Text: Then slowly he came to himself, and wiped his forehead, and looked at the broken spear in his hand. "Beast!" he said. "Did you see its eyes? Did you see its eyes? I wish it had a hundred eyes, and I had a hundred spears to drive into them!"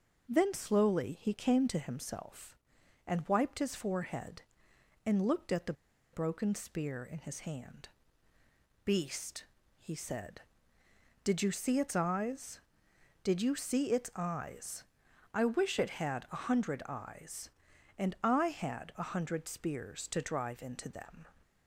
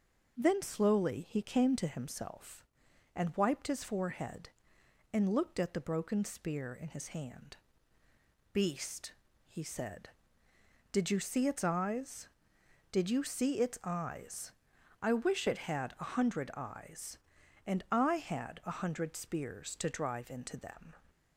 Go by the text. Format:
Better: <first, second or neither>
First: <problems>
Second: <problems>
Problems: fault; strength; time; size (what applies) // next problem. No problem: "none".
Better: second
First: pauses between "the" and "broken"; at 5.7 s; 0.40 s long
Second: none